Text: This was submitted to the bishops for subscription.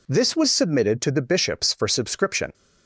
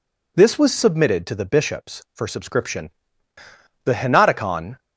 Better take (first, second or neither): first